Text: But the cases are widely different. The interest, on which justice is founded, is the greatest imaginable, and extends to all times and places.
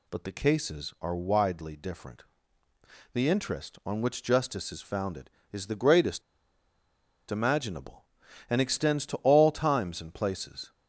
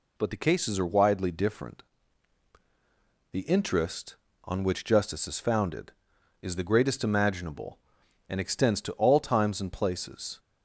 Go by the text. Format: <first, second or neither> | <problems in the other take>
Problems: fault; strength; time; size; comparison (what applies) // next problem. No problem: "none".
second | pauses between "greatest" and "imaginable"; at 6.2 s; 1.0 s long